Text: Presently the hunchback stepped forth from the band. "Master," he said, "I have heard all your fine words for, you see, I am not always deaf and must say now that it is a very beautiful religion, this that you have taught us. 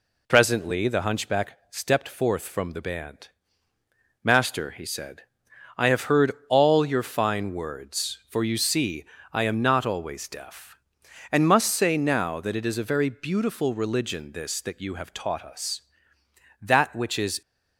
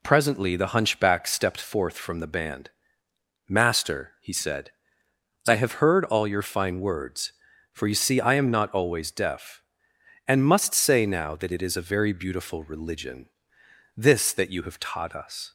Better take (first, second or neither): second